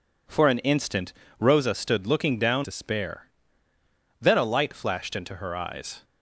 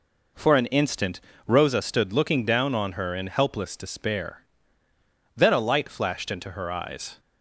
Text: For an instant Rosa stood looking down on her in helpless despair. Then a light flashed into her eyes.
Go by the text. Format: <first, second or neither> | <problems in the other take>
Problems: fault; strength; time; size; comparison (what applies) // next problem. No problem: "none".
second | pauses between "instant" and "Rosa"; slight; at 1.1 s; 0.26 s long; slight in the second // skips "on her in helpless"; at 2.6 s